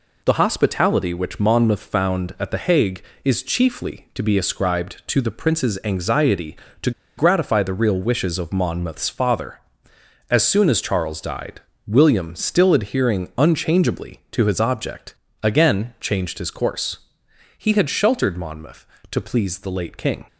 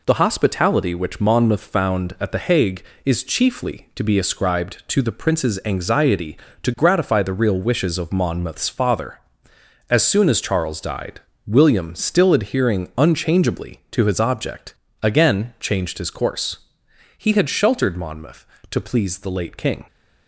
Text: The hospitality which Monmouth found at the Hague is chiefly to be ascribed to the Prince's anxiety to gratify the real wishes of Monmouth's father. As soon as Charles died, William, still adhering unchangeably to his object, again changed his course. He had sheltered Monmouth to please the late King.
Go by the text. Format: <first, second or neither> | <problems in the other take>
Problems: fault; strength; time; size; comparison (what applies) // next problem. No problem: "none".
second | pauses between "to" and "gratify"; slight; at 6.9 s; 0.26 s long